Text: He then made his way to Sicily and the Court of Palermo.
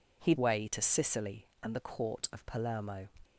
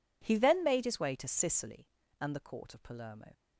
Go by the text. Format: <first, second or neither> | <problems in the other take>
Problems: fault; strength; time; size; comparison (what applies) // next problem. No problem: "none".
second | skips "then made his"; at 0.3 s